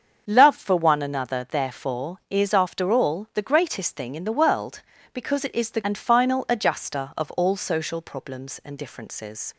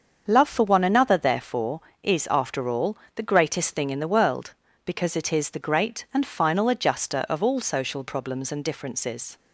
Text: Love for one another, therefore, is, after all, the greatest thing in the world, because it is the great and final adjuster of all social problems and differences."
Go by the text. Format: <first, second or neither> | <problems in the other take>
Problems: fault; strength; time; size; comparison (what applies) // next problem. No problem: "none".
second | starts louder than the rest; until 1.2 s; 7 dB; also in the second // skips "great"; at 5.8 s